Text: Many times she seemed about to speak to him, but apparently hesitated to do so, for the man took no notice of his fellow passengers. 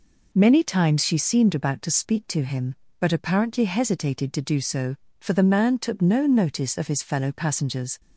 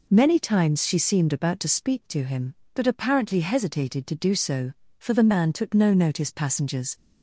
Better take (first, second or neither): first